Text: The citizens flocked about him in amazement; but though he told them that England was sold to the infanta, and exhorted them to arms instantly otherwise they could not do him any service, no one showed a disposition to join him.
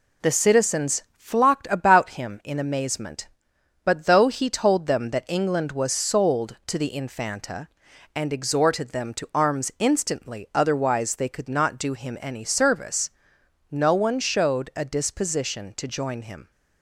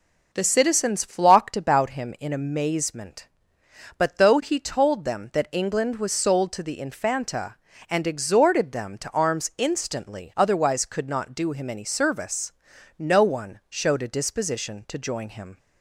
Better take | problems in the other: first | skips "they"; at 10.8 s

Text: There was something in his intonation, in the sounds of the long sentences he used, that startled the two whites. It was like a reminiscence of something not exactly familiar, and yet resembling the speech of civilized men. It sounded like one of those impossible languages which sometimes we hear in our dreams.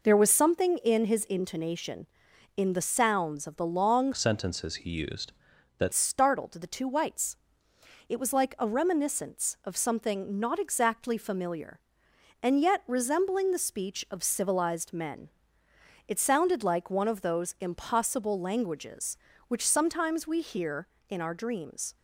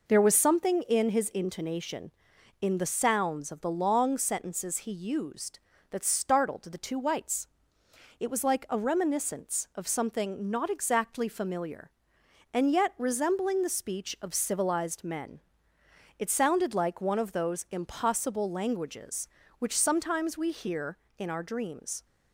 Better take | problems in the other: second | changes voice from "sentences" to "that"; from 4.1 to 5.9 s; 1.8 s long

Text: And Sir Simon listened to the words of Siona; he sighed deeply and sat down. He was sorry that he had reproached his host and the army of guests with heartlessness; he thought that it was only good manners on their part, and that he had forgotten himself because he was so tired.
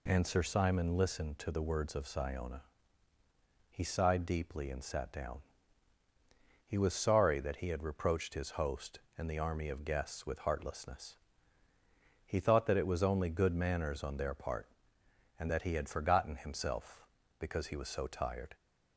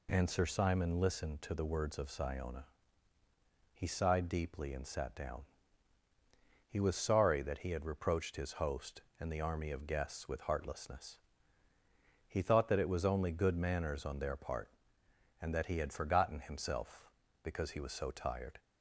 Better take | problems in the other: neither | none

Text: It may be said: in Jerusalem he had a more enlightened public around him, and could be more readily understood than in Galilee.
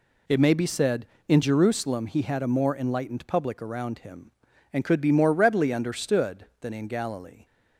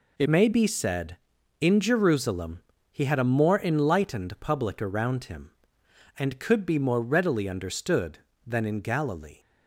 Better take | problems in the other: first | changes voice at "may"; from 0.2 s on; 9.1 s long // pauses between "Jerusalem" and "he"; slight; at 2.5 s; 0.30 s long

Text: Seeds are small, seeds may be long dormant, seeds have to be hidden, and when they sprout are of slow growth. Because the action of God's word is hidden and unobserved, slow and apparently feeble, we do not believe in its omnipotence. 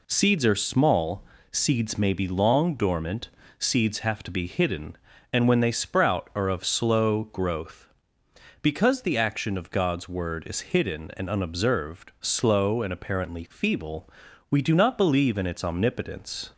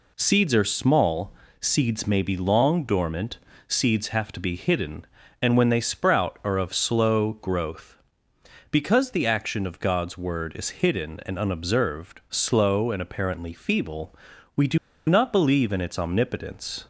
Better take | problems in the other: first | pauses between "do" and "not"; slight; at 14.7 s; 0.30 s long

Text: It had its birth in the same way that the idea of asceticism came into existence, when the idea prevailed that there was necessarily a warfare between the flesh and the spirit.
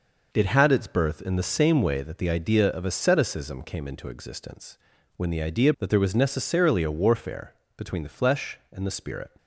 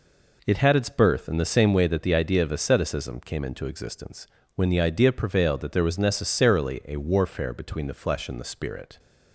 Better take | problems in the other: second | skips "prevailed"; at 5.7 s // pauses between "warfare" and "between"; slight; at 7.5 s; 0.24 s long

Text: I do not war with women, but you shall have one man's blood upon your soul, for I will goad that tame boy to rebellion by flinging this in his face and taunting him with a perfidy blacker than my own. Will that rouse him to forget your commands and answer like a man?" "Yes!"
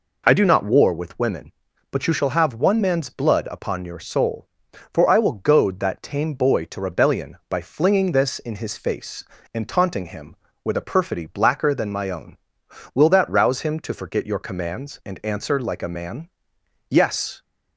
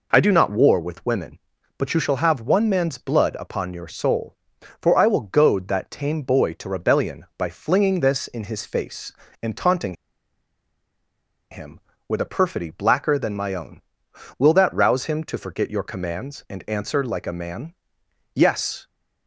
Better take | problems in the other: first | pauses between "taunting" and "him"; strong; at 9.9 s; 1.5 s long

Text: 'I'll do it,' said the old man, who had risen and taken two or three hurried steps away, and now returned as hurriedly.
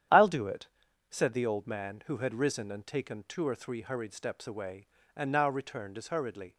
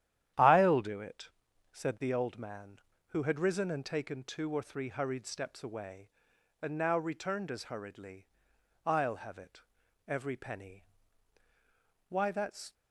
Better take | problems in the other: first | starts louder than the rest; strong; until 1.7 s; 11 dB; strong in the first // goes on to say "I'll have it every penny Why that's"; strong; from 8.8 s on; 3.8 s long

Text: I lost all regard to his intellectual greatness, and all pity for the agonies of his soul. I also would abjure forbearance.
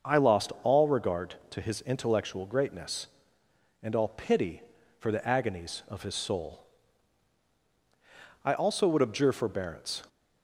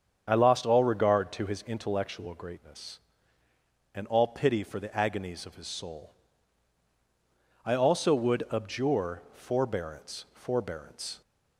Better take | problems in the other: first | starts louder than the rest; strong; until 1.2 s; 8 dB; also in the first // says "forbearance" twice; at 10.3 s

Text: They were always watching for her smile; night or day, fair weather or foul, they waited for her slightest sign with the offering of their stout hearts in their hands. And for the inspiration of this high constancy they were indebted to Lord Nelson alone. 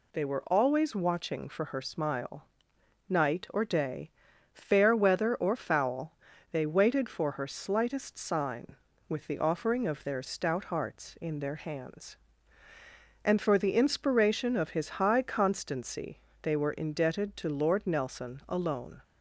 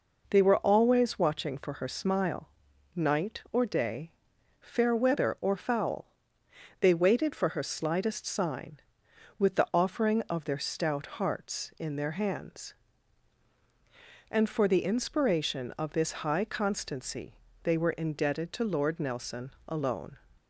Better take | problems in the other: second | says "his" for "this"; at 14.7 s // pauses between "constancy" and "they"; slight; at 16.2 s; 0.22 s long; slight in the second

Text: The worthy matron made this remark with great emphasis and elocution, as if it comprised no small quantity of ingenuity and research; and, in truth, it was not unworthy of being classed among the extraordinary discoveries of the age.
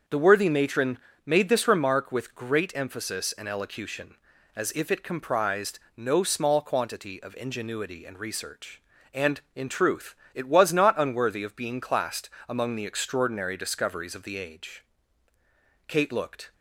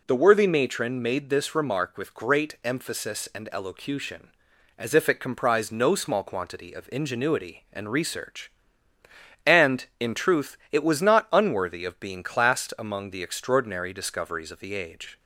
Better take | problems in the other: second | starts louder than the rest; until 1.3 s; 6.5 dB // pauses between "matron" and "made"; slight; at 0.9 s; 0.26 s long // pauses between "comprised" and "no"; slight; at 5.8 s; 0.16 s long // pauses between "classed" and "among"; slight; at 12.2 s; 0.18 s long // goes on to say "Kate looked"; noticeable; from 15.8 s on; 0.64 s long

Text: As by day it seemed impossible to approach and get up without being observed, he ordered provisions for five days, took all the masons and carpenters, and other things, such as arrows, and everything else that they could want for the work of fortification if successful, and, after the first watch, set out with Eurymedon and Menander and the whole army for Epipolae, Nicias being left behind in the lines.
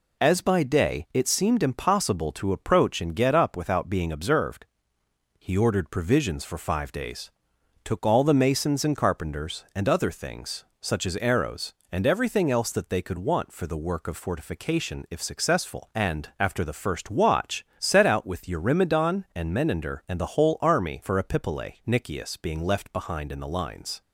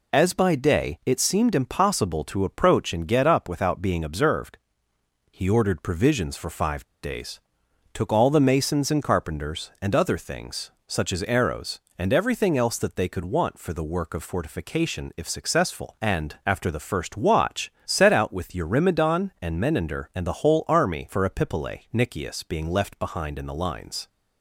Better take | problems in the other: first | pauses between "five" and "days"; slight; at 6.8 s; 0.20 s long

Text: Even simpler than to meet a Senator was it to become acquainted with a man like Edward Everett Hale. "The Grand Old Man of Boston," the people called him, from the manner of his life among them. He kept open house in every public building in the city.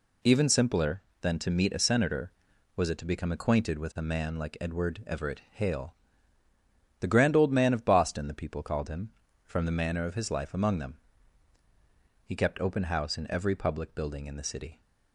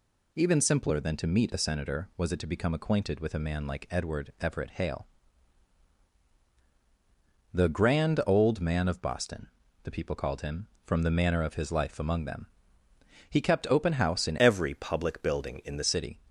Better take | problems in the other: first | changes voice from "every" to "the"; from 14.3 to 15.8 s; 1.5 s long

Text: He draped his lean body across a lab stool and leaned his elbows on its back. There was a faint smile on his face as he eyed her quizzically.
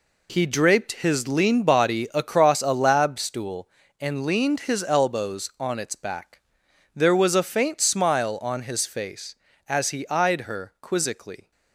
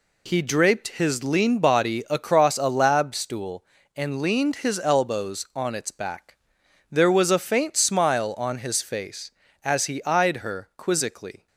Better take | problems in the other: second | gets quieter; strong; throughout; 9.5 dB

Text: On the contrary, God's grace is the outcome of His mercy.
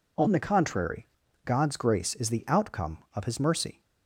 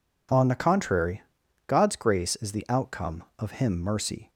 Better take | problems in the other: first | says "Him" for "His"; at 3.5 s

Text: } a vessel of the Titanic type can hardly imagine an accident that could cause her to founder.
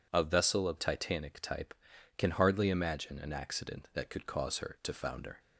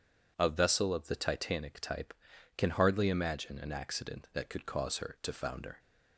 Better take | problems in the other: second | skips "the"; at 0.7 s

